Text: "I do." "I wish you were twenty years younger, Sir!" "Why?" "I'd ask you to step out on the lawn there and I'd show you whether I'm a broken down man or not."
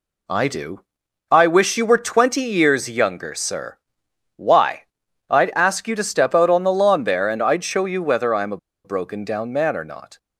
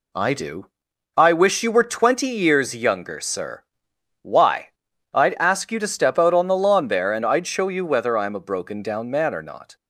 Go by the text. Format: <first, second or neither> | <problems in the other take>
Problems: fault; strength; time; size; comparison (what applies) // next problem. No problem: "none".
second | pauses between "a" and "broken"; slight; at 8.5 s; 0.28 s long